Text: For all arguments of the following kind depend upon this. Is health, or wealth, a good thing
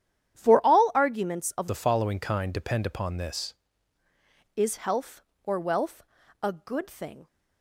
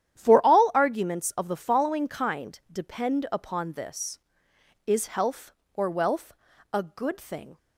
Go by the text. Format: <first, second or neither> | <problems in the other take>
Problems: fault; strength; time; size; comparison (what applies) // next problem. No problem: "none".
second | starts louder than the rest; strong; until 1.4 s; 10 dB; strong in the second // changes voice from "the" to "this"; from 1.6 to 3.5 s; 1.9 s long